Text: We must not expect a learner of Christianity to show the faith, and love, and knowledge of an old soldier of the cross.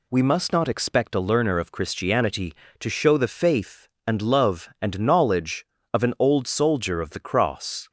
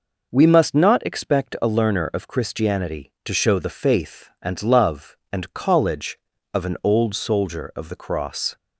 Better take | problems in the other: first | says "college" for "knowledge"; at 5.5 s

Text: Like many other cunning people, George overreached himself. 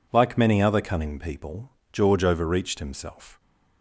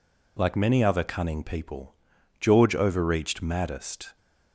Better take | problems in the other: first | says "maddest" for "himself"; at 3.4 s

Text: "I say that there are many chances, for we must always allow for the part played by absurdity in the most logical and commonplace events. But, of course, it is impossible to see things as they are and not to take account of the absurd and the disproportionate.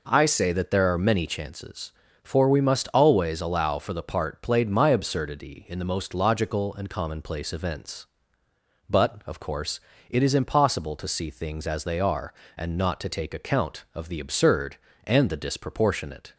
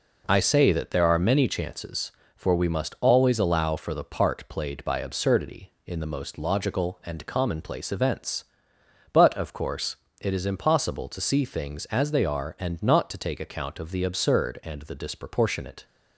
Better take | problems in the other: second | says "my" for "by"; at 4.6 s

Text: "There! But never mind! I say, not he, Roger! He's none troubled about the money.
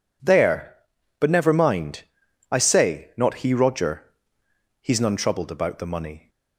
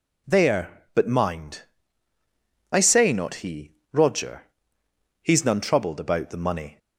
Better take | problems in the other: first | skips "never"; at 1.0 s

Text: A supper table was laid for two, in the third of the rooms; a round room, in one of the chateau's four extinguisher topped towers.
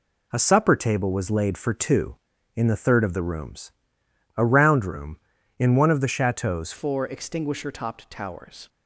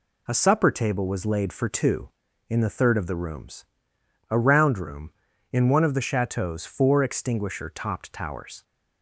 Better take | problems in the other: second | changes voice at "four"; from 6.7 s on; 1.9 s long

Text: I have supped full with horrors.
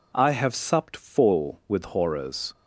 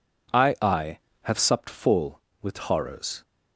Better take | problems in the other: first | says "I" twice; at 0.6 s

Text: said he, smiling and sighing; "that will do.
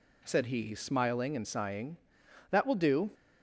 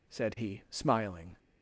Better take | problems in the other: first | stops before "and sighing that will do"; at 1.3 s

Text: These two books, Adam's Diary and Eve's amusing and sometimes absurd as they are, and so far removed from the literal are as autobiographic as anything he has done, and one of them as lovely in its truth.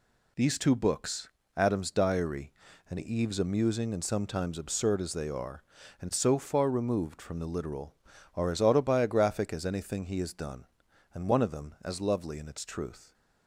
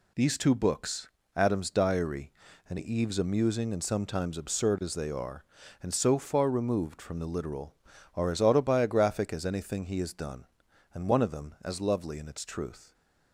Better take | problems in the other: neither | none

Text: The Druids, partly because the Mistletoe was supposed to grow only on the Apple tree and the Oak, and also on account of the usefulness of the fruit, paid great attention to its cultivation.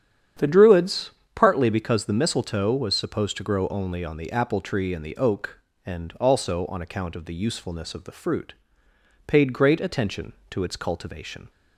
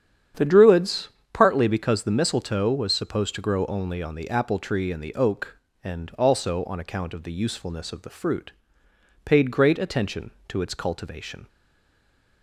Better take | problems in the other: first | starts louder than the rest; strong; until 1.6 s; 9 dB; strong in the first // stays silent after the last word; slight; from 11.4 s on; 1.0 s long

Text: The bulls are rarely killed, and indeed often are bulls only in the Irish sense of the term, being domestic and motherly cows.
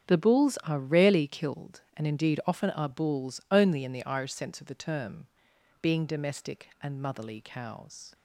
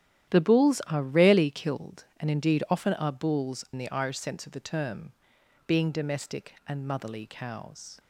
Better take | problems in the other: first | starts louder than the rest; strong; until 1.3 s; 11 dB; strong in the first // skips "only"; at 3.6 s

